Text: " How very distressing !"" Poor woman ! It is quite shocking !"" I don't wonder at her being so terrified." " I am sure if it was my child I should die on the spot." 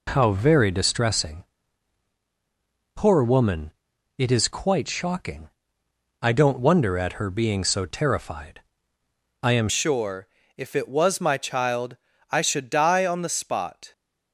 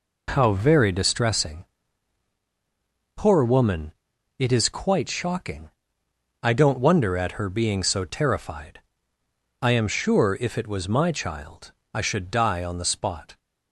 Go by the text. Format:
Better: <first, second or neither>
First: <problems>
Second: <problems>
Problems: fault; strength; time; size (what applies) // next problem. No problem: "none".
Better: second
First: changes voice at "sure"; from 9.6 s on; 4.3 s long // pauses between "sure" and "if"; slight; at 10.2 s; 0.28 s long // pauses between "child" and "I"; slight; at 11.9 s; 0.32 s long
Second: pauses between "child" and "I"; slight; at 11.7 s; 0.22 s long